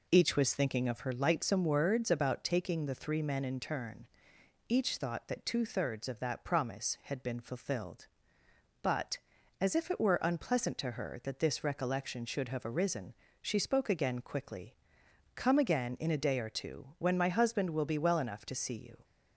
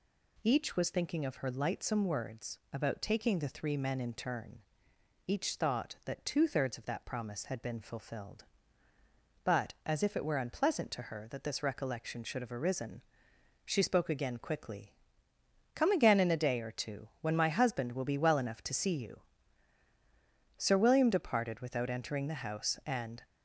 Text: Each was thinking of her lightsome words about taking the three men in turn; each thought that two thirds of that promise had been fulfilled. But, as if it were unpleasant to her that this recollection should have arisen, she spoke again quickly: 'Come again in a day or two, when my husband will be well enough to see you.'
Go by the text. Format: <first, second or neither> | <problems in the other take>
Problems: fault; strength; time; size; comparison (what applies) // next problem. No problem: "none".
first | goes on to say "Sir William departed without entering the house and"; strong; from 20.5 s on; 2.6 s long